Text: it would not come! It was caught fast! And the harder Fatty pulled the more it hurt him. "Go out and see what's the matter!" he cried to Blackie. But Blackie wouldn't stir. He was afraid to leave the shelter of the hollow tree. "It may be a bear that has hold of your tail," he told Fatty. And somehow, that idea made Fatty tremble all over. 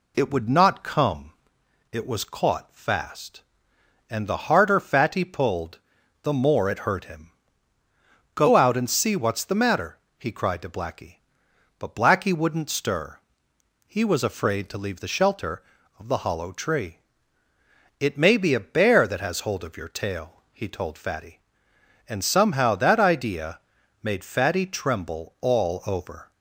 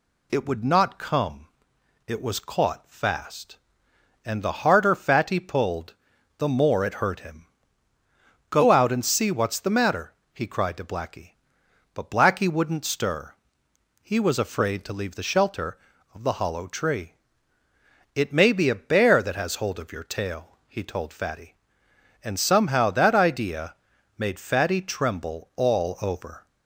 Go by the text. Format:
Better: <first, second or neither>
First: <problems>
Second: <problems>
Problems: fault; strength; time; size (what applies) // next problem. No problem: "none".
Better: second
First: starts louder than the rest; slight; until 1.7 s; 2 dB // pauses between "pulled" and "the"; at 5.7 s; 0.42 s long // pauses between "idea" and "made"; at 23.5 s; 0.42 s long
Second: pauses between "pulled" and "the"; at 5.9 s; 0.42 s long // pauses between "idea" and "made"; at 23.7 s; 0.42 s long